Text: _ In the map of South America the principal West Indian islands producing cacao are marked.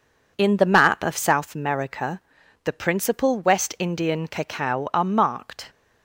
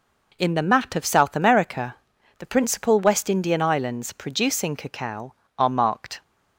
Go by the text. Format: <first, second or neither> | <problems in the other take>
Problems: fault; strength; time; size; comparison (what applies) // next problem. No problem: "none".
second | pauses between "America" and "the"; at 2.1 s; 0.44 s long; also in the second // skips "islands producing"; at 4.2 s